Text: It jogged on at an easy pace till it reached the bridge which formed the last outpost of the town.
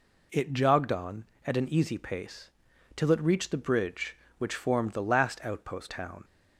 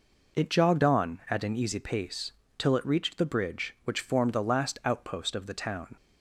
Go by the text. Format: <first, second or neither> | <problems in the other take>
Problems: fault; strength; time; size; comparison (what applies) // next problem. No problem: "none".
second | pauses between "pace" and "till"; at 2.5 s; 0.44 s long; slight in the second // skips "of the"; at 5.8 s